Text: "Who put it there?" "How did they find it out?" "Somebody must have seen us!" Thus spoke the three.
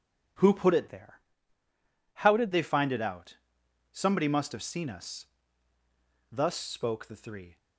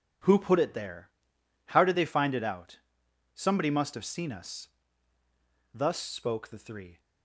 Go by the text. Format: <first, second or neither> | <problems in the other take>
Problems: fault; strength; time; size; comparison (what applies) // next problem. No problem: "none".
second | changes voice from "there" to "did"; from 0.8 to 2.5 s; 1.7 s long